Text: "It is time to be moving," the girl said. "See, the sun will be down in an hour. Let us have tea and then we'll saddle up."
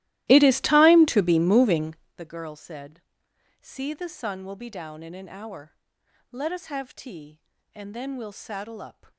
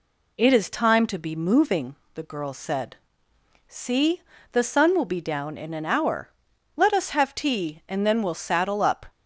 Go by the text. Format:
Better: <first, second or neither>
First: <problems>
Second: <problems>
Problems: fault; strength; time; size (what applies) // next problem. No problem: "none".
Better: second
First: starts louder than the rest; strong; until 2.2 s; 16 dB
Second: none